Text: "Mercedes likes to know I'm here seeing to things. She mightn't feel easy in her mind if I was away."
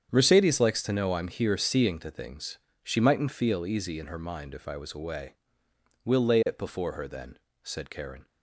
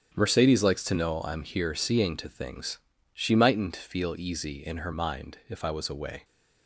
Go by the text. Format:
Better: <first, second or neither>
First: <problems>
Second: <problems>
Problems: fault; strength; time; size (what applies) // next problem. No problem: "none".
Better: second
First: starts louder than the rest; strong; until 1.1 s; 8 dB // goes on to say "We'll lay it before her then said Karen"; strong; from 6.0 s on; 2.2 s long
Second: starts louder than the rest; strong; until 1.1 s; 9 dB